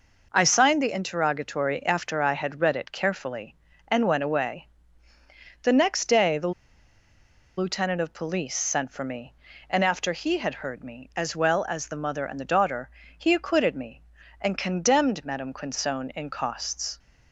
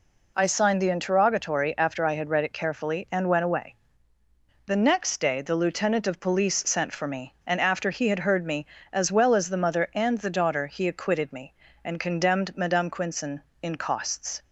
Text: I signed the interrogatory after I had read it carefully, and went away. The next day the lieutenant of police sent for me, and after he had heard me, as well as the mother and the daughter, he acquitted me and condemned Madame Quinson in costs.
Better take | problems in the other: second | pauses between "the" and "lieutenant"; at 6.5 s; 1.0 s long

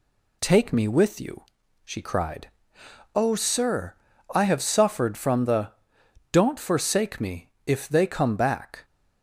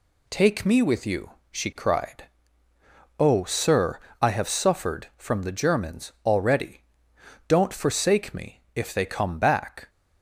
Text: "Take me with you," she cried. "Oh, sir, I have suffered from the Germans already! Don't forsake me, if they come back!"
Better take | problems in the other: second | skips "Germans already"; at 6.0 s

